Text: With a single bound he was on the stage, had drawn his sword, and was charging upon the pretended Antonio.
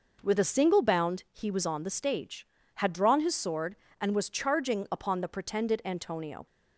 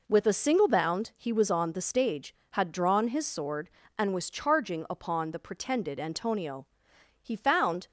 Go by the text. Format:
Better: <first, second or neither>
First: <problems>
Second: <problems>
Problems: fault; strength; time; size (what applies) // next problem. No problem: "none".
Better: first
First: none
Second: goes on to say "He found"; noticeable; from 7.2 s on; 0.64 s long